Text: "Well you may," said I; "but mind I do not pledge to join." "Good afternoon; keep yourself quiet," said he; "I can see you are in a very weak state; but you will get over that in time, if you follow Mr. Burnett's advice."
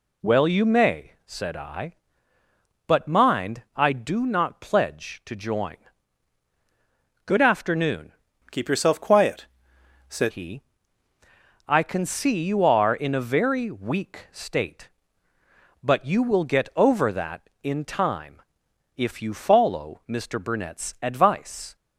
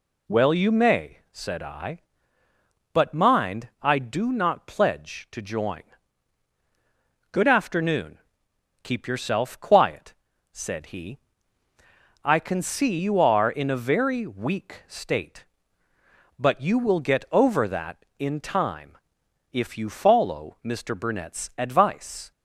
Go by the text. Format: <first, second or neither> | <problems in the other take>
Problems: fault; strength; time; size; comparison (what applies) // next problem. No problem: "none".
second | changes voice from "keep" to "said"; from 8.4 to 10.3 s; 1.9 s long